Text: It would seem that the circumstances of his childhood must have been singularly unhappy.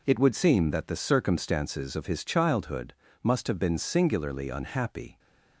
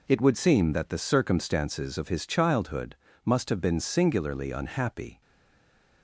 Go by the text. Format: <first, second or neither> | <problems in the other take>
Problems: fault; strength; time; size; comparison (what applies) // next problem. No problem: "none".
first | pauses between "childhood" and "must"; slight; at 2.9 s; 0.30 s long; slight in the first // stays silent after the last word; slight; from 5.2 s on; 0.8 s long